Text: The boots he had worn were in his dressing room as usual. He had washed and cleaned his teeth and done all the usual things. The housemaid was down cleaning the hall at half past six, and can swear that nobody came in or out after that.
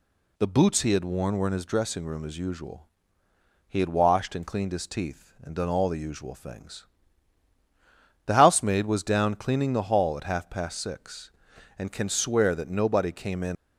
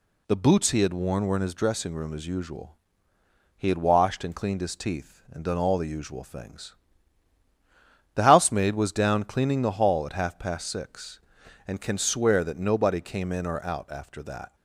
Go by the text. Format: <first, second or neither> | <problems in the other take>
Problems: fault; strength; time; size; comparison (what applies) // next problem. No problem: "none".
second | stops before "or out after that"; at 13.5 s